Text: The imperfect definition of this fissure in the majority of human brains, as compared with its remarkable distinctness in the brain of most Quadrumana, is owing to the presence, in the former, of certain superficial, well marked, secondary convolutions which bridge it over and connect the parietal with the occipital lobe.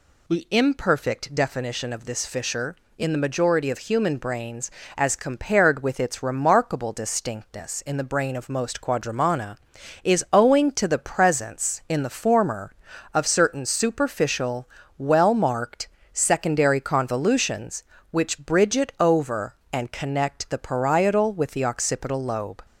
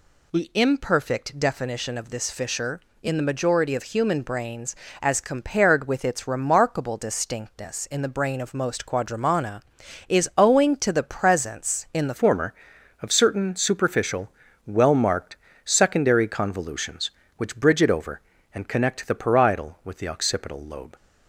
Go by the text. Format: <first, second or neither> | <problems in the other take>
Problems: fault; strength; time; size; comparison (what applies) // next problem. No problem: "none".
first | changes voice at "former"; from 12.1 s on; 8.8 s long